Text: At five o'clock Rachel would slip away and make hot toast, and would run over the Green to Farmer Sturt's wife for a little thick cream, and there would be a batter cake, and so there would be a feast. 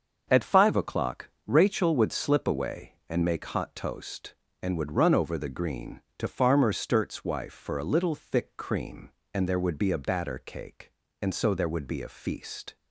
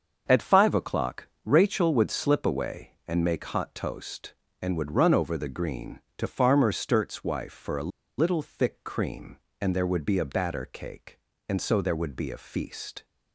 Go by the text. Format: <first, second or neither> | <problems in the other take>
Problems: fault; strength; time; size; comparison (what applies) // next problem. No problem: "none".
first | starts louder than the rest; until 1.2 s; 7 dB; also in the first // pauses between "o'clock" and "Rachel"; slight; at 1.2 s; 0.16 s long; slight in the first // pauses between "a" and "little"; slight; at 7.9 s; 0.30 s long